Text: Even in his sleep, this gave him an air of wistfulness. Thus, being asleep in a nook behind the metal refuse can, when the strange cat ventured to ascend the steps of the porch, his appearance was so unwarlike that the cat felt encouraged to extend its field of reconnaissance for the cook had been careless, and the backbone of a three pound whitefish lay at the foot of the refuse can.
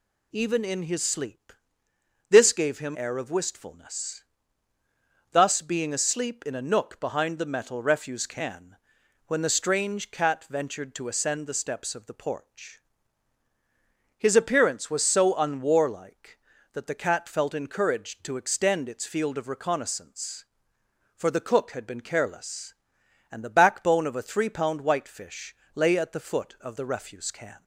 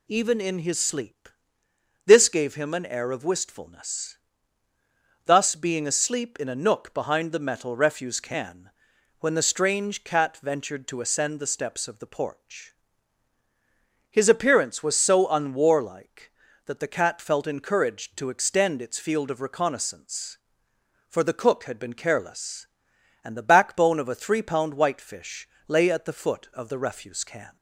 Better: second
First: skips "an"; at 2.9 s // pauses between "whitefish" and "lay"; slight; at 25.5 s; 0.18 s long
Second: pauses between "whitefish" and "lay"; slight; at 25.4 s; 0.18 s long

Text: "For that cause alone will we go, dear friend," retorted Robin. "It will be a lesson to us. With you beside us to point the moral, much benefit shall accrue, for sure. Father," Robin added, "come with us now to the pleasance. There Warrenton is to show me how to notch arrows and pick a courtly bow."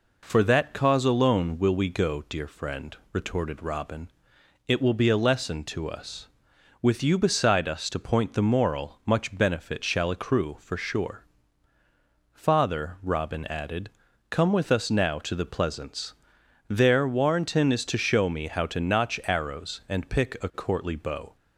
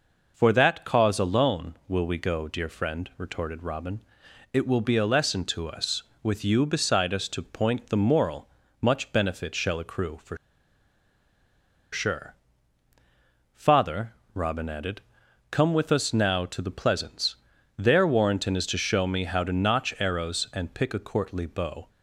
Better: first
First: none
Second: pauses between "for" and "sure"; strong; at 10.3 s; 1.5 s long

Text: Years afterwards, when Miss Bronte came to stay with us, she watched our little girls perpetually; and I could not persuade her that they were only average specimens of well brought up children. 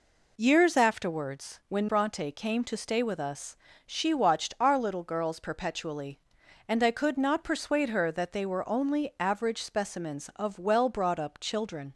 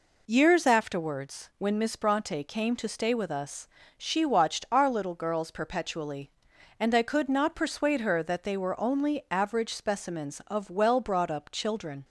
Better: second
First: skips "Miss"; at 1.8 s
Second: none

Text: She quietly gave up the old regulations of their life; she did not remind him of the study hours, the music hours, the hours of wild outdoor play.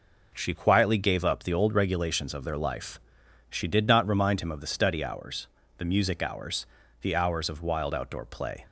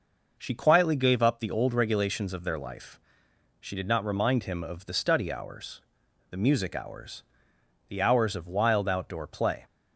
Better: neither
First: none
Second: none

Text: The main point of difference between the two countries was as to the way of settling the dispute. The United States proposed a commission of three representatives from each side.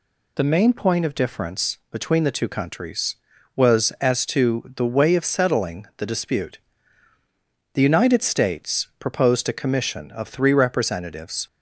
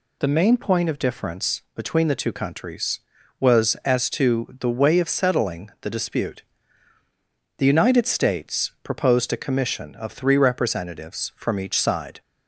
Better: second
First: stops before "from each side"; at 11.4 s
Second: none

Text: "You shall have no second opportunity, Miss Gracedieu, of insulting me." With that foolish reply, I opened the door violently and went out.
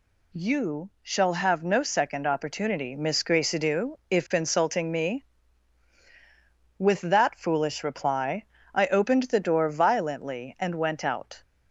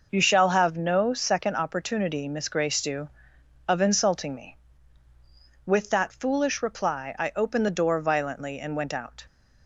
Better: second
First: says "if" for "of"; at 4.0 s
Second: none

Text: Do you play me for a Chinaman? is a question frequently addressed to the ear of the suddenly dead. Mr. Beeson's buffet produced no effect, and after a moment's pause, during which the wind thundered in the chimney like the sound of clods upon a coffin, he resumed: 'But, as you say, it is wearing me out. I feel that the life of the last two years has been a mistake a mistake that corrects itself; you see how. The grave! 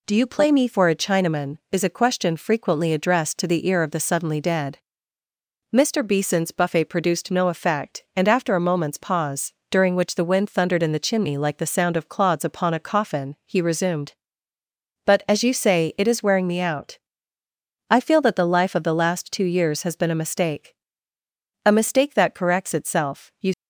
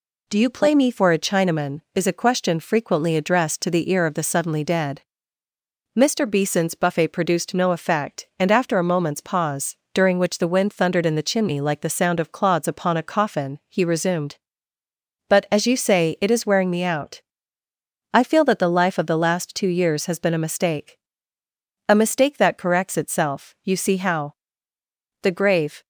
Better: second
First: pauses between "mistake" and "a"; noticeable; at 20.7 s; 0.88 s long // stops before "see how The grave"; at 23.5 s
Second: pauses between "mistake" and "a"; noticeable; at 20.9 s; 0.88 s long

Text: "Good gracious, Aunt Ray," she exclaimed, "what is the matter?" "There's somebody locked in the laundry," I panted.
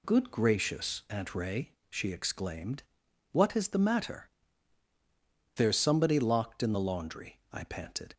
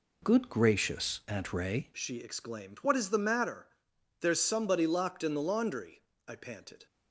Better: first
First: none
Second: changes voice at "she"; from 1.9 s on; 4.9 s long

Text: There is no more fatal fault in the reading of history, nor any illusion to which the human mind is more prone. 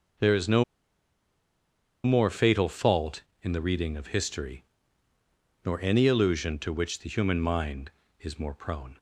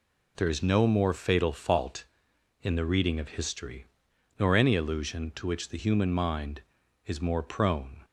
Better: second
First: pauses between "no" and "more"; strong; at 0.6 s; 1.4 s long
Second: none

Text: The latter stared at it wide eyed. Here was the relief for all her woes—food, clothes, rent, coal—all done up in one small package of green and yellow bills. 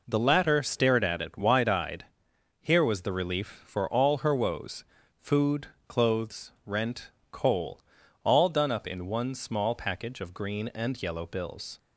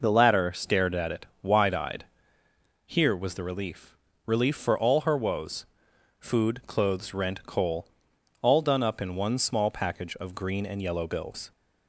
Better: first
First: none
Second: pauses between "it" and "wide"; slight; at 1.2 s; 0.16 s long // says "relief" twice; at 4.2 s

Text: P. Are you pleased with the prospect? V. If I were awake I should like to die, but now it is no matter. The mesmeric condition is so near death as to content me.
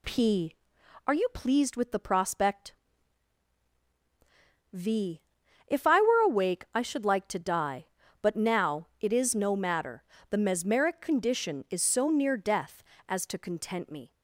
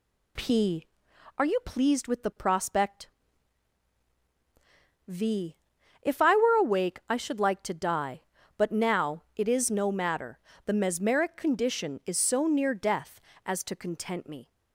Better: neither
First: none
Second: none

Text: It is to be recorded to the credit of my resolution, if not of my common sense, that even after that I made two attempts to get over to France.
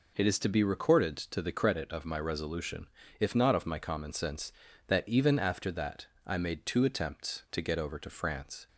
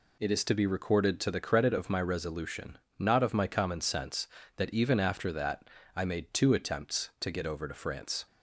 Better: first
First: pauses between "that" and "I"; slight; at 6.0 s; 0.20 s long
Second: skips "if"; at 2.8 s // pauses between "that" and "I"; slight; at 5.6 s; 0.28 s long

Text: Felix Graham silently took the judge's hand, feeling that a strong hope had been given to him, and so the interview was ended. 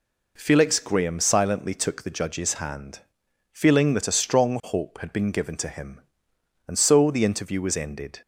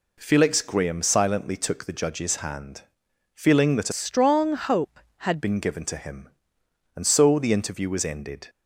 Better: first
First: none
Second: changes voice from "strong" to "had"; from 3.9 to 5.4 s; 1.5 s long

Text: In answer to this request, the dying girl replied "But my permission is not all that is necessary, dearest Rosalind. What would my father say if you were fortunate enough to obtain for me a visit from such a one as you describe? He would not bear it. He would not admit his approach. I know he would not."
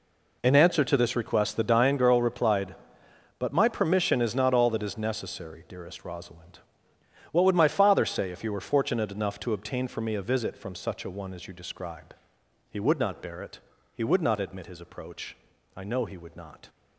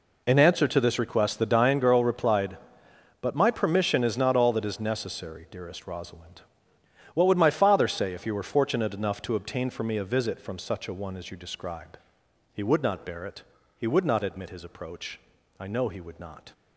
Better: neither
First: none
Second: none

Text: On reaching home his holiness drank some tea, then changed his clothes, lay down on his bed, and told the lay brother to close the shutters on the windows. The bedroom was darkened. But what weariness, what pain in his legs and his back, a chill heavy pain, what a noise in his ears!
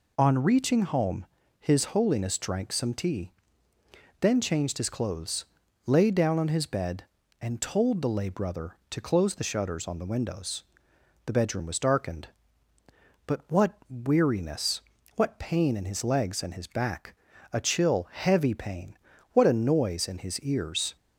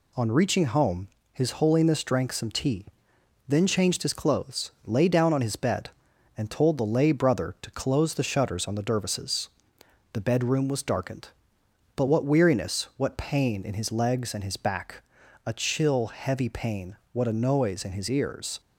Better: first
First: pauses between "home" and "his"; slight; at 1.2 s; 0.34 s long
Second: pauses between "home" and "his"; slight; at 1.0 s; 0.24 s long // says "dervises" for "windows"; at 8.8 s

